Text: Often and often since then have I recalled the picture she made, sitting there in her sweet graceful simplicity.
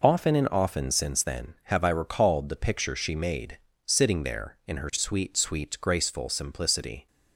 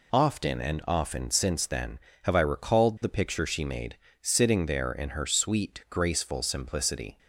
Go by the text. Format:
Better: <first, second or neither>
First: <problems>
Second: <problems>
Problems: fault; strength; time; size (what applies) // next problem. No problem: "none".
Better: second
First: says "sweet" twice; at 5.3 s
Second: none